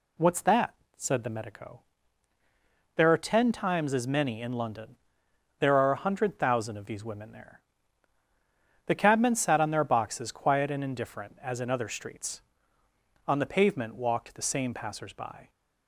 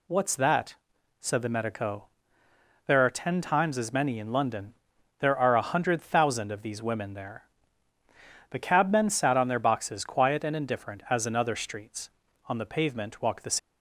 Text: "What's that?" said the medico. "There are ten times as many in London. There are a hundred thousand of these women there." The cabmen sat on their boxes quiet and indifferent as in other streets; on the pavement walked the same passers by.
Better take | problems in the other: first | stops before "same passers by"; at 13.5 s

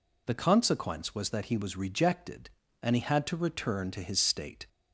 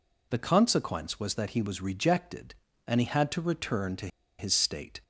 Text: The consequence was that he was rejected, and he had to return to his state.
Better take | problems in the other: first | pauses between "to" and "his"; slight; at 4.0 s; 0.31 s long

